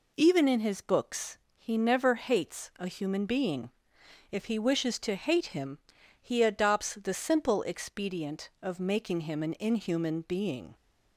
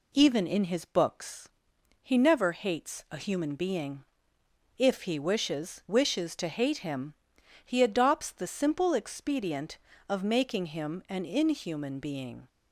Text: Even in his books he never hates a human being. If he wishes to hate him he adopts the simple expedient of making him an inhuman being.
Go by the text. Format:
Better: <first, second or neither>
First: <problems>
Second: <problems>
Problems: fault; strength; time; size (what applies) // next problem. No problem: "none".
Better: first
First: pauses between "books" and "he"; slight; at 1.3 s; 0.18 s long // pauses between "him" and "he"; at 5.7 s; 0.42 s long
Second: pauses between "books" and "he"; noticeable; at 1.4 s; 0.54 s long // says "wishes" twice; at 5.8 s // pauses between "him" and "he"; noticeable; at 7.1 s; 0.50 s long